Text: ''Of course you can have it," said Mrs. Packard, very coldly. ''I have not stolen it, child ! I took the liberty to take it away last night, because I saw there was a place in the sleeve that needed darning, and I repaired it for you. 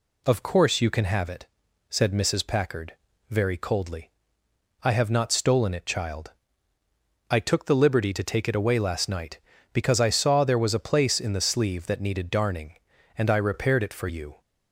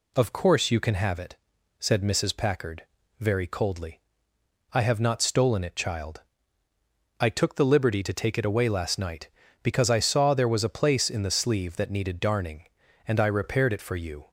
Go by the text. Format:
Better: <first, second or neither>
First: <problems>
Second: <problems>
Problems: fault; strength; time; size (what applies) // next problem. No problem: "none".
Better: neither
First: none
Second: none